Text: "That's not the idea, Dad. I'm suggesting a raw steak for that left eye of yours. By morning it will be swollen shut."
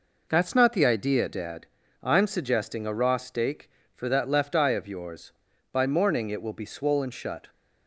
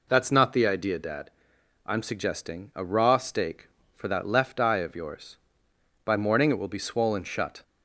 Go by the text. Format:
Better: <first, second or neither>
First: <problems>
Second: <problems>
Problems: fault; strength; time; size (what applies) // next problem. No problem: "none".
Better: neither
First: none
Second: none